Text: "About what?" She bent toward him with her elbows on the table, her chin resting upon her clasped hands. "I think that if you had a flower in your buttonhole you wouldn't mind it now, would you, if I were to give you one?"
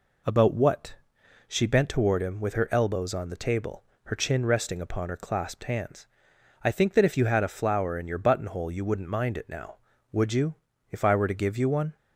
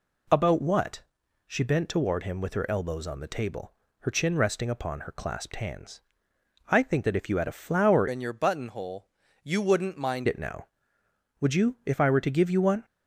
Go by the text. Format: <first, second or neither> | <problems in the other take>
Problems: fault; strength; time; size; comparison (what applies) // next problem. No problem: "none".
first | changes voice from "in" to "mind"; from 8.0 to 10.2 s; 2.2 s long // pauses between "buttonhole" and "you"; slight; at 9.0 s; 0.32 s long